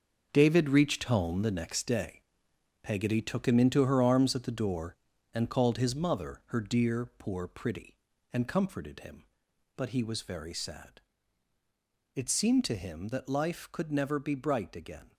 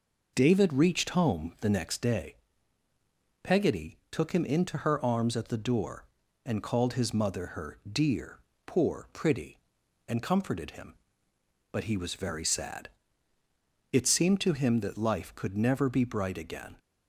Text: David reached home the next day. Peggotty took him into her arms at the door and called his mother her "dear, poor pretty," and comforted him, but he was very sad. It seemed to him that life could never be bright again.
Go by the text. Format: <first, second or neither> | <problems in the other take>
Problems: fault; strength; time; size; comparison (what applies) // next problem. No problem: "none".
second | gets quieter; strong; throughout; 9.5 dB